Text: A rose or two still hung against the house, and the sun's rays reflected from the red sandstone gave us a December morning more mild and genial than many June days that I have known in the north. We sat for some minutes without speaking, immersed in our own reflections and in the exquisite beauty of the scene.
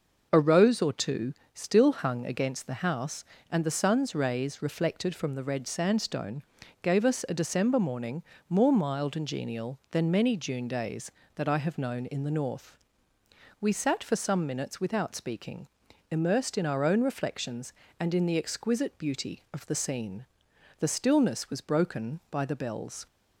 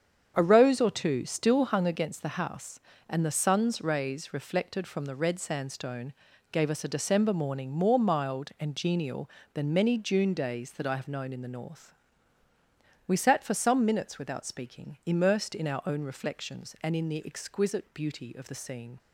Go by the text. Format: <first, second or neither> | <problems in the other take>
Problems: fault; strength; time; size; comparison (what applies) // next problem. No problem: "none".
second | starts louder than the rest; noticeable; until 1.3 s; 6 dB; strong in the second // pauses between "two" and "still"; slight; at 1.3 s; 0.22 s long // pauses between "sandstone" and "gave"; at 6.4 s; 0.40 s long; also in the second // pauses between "morning" and "more"; slight; at 8.2 s; 0.26 s long // goes on to say "The stillness was broken by the bells"; strong; from 20.7 s on; 2.2 s long